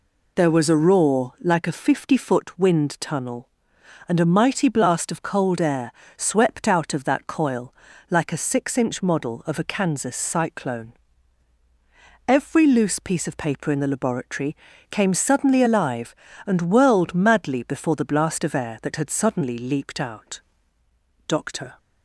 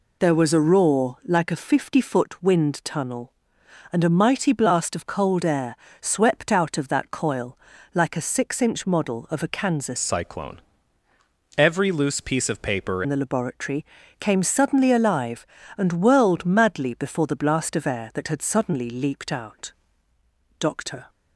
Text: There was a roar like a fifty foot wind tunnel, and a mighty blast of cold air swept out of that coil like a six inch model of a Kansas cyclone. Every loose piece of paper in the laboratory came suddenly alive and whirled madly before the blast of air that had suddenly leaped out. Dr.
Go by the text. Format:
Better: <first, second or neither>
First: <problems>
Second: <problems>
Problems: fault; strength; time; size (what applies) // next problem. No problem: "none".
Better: first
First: pauses between "air" and "swept"; slight; at 5.8 s; 0.26 s long // pauses between "coil" and "like"; slight; at 7.7 s; 0.36 s long // pauses between "laboratory" and "came"; at 14.5 s; 0.38 s long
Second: pauses between "air" and "swept"; slight; at 5.7 s; 0.26 s long // pauses between "coil" and "like"; slight; at 7.5 s; 0.36 s long // changes voice from "cyclone" to "paper"; from 9.9 to 13.0 s; 3.1 s long // pauses between "laboratory" and "came"; at 13.8 s; 0.38 s long